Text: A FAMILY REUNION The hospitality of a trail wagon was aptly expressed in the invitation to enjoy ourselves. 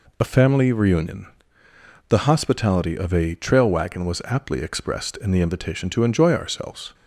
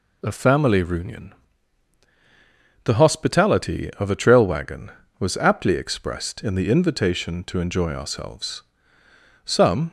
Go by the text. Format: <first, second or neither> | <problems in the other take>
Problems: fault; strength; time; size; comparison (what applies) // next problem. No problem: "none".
first | pauses between "REUNION" and "The"; strong; at 1.3 s; 1.5 s long; noticeable in the first // goes on to say "Some"; slight; from 9.4 s on; 0.44 s long